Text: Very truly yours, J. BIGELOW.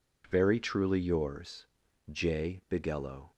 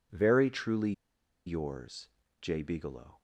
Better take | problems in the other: first | pauses between "truly" and "yours"; noticeable; at 0.9 s; 0.54 s long

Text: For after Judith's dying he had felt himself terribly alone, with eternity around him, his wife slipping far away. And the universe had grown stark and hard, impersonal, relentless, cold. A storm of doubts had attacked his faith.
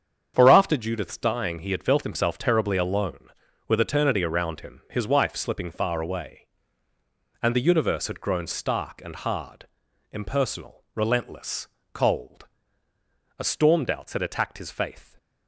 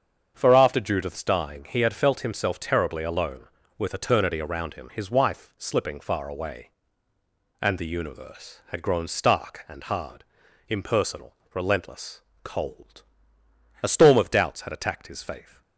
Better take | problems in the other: second | starts louder than the rest; strong; until 1.3 s; 8 dB; strong in the second // skips "of"; at 13.8 s

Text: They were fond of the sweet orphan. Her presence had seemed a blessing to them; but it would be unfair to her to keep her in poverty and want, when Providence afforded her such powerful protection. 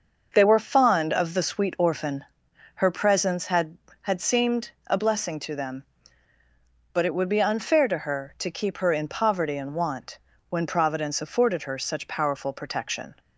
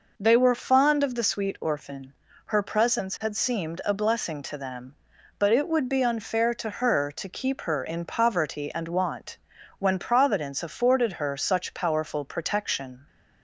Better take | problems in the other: second | starts louder than the rest; until 1.3 s; 6.5 dB // says "had" twice; at 4.0 s // pauses between "seemed" and "a"; slight; at 4.7 s; 0.16 s long

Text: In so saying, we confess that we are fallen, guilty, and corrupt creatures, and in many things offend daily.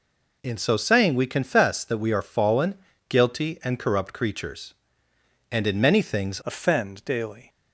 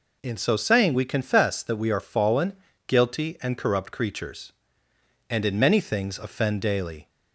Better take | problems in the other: second | changes voice at "offend"; from 6.4 s on; 1.0 s long

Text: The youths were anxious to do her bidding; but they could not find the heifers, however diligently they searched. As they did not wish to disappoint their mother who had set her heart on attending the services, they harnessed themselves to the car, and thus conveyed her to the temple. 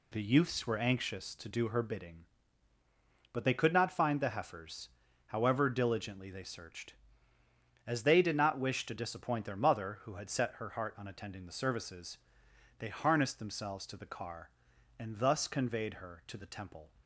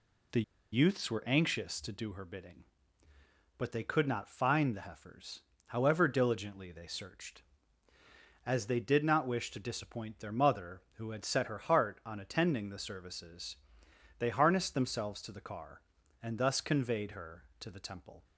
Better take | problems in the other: first | pauses between "The" and "youths"; slight; at 0.4 s; 0.30 s long

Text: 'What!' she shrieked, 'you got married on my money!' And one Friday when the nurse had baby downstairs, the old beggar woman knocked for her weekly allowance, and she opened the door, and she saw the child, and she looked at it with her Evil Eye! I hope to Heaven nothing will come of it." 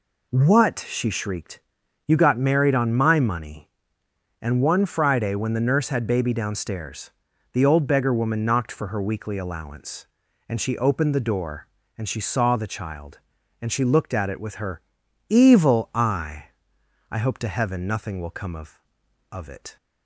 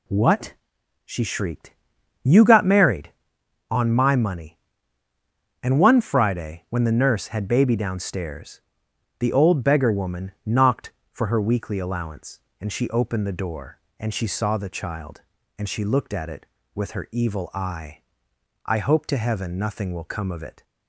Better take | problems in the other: second | pauses between "her" and "Evil"; noticeable; at 14.8 s; 0.46 s long // says "of" twice; at 19.3 s

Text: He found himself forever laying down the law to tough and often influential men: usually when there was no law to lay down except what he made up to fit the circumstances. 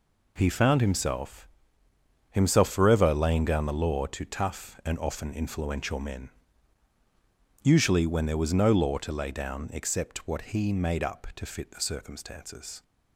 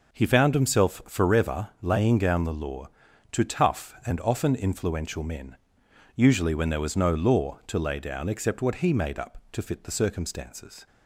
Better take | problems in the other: second | says "himself" twice; at 2.2 s

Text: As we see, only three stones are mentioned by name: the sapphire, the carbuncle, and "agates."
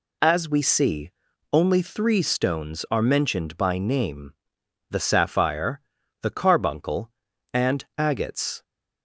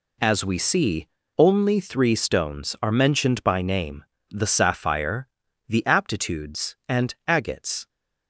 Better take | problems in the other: first | says "aptitudes" for "carbuncle"; at 5.8 s

